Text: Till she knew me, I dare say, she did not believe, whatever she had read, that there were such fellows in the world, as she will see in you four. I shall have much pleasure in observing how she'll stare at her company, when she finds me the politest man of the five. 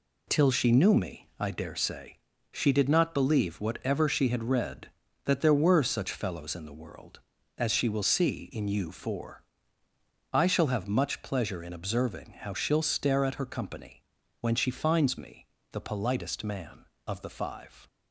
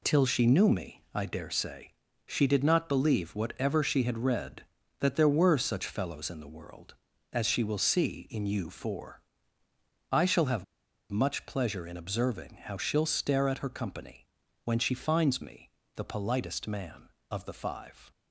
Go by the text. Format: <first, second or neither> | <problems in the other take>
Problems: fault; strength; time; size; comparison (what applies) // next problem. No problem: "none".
first | pauses between "have" and "much"; at 10.6 s; 0.45 s long // pauses between "me" and "the"; slight; at 15.7 s; 0.24 s long; slight in the first